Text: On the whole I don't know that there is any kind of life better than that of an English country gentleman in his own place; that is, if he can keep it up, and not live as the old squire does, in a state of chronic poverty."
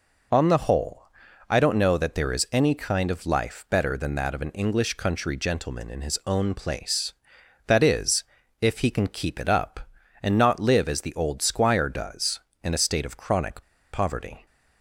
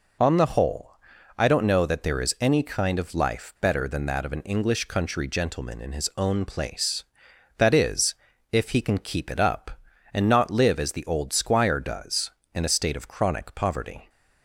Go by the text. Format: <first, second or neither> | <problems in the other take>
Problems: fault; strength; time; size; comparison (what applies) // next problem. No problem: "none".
second | pauses between "whole" and "I"; at 1.0 s; 0.44 s long; also in the second // pauses between "chronic" and "poverty"; slight; at 13.6 s; 0.29 s long